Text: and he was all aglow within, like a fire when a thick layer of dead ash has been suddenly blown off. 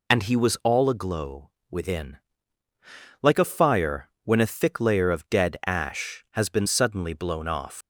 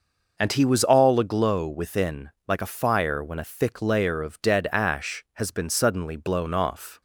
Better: second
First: pauses between "aglow" and "within"; slight; at 1.4 s; 0.20 s long // pauses between "fire" and "when"; slight; at 4.0 s; 0.16 s long // leaves "off" unfinished; at 7.8 s; 100 ms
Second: none

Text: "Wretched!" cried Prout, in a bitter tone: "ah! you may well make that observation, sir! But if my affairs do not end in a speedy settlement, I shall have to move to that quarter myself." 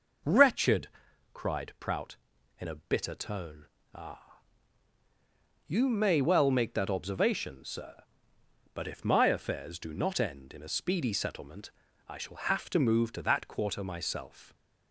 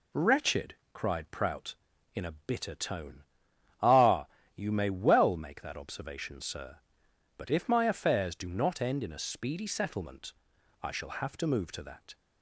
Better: first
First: none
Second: stops before "quarter myself"; at 12.1 s

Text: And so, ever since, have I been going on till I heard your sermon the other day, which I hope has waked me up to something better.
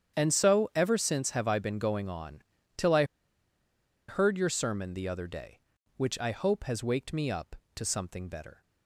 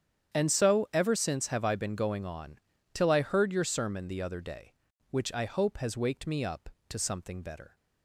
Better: second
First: starts louder than the rest; strong; until 1.2 s; 9 dB // pauses between "on" and "till"; slight; at 2.4 s; 0.34 s long // pauses between "I" and "heard"; at 3.0 s; 1.0 s long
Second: starts louder than the rest; strong; until 1.4 s; 9 dB // pauses between "on" and "till"; slight; at 2.5 s; 0.34 s long

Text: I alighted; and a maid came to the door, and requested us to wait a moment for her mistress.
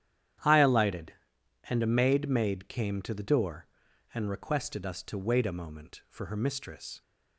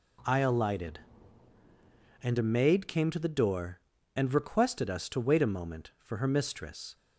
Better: second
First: starts louder than the rest; strong; until 2.0 s; 10.5 dB // says "maid" twice; at 2.2 s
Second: none

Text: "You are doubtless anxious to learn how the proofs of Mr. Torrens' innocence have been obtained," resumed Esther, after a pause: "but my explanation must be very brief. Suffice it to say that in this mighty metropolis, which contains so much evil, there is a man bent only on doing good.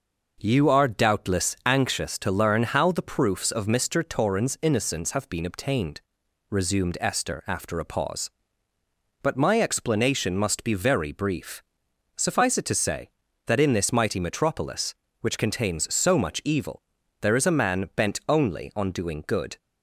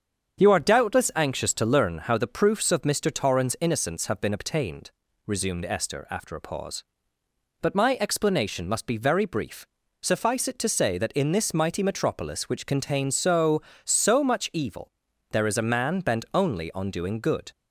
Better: first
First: none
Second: starts louder than the rest; strong; until 1.4 s; 7.5 dB // says "so" twice; at 13.8 s

